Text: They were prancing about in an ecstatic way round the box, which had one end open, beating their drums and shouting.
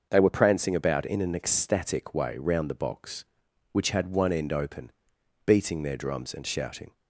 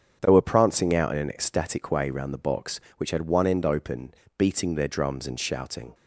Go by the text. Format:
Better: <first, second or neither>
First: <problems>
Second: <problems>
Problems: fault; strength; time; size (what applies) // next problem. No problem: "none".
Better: first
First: starts louder than the rest; until 1.1 s; 6.5 dB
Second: starts louder than the rest; strong; until 1.2 s; 7.5 dB // says "out" for "about"; at 0.9 s